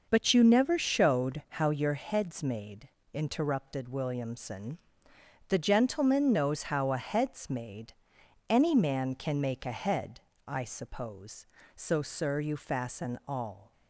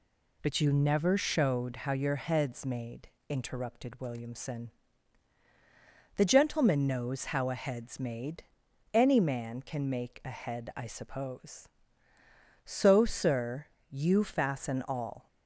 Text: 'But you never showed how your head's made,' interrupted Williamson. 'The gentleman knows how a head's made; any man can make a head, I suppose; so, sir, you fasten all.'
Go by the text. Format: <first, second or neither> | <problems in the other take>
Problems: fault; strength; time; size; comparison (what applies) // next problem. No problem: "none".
neither | none